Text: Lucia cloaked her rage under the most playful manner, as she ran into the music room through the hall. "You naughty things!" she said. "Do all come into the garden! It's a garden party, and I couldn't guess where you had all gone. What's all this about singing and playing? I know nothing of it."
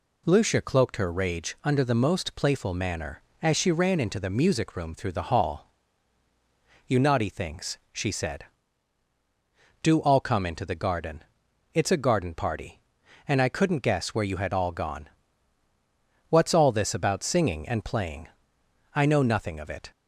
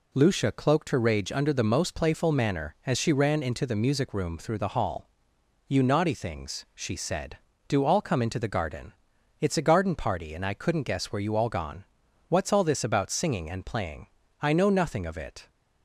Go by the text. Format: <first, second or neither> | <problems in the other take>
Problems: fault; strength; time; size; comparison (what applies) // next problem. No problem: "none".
first | skips "had"; at 11.3 s